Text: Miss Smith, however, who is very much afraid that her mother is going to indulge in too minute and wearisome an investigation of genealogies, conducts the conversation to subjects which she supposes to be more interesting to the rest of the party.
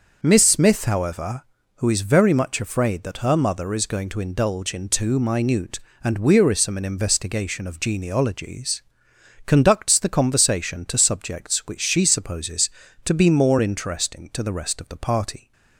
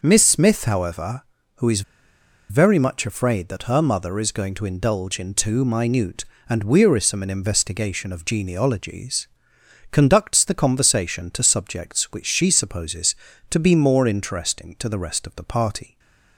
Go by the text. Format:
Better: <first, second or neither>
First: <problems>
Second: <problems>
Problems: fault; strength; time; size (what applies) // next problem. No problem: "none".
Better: first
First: none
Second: pauses between "is" and "very"; noticeable; at 1.8 s; 0.68 s long // stays silent after the last word; slight; from 15.8 s on; 0.5 s long